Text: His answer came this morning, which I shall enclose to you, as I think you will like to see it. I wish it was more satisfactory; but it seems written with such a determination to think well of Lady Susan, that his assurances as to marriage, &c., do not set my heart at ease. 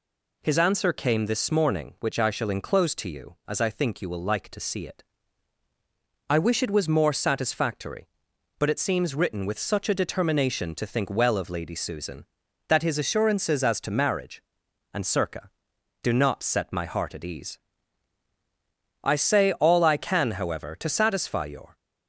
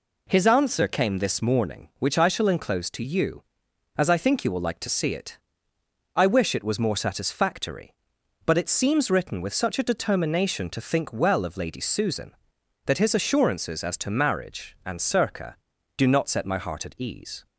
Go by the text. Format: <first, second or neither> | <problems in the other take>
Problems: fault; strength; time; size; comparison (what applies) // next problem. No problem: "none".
second | goes on to say "I say all I can however to satisfy your"; strong; from 19.0 s on; 2.7 s long